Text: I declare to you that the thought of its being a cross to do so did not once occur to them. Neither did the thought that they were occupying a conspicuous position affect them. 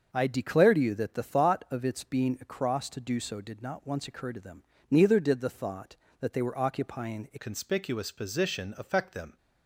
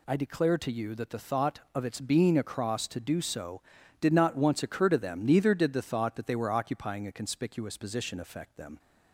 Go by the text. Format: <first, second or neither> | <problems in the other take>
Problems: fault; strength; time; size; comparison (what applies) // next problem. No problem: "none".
second | starts louder than the rest; until 1.1 s; 6.5 dB // changes voice at "conspicuous"; from 7.3 s on; 2.0 s long